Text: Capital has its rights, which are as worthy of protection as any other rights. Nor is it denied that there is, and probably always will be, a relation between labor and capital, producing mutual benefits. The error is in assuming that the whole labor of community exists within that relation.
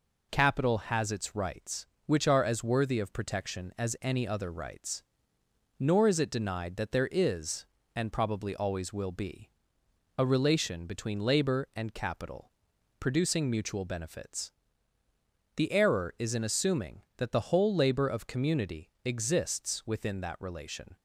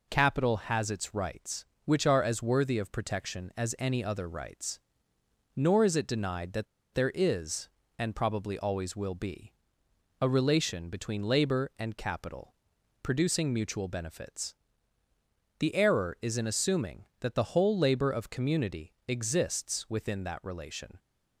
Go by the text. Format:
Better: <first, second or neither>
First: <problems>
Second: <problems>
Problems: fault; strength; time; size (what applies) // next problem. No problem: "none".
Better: first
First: none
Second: pauses between "that" and "there"; slight; at 6.6 s; 0.28 s long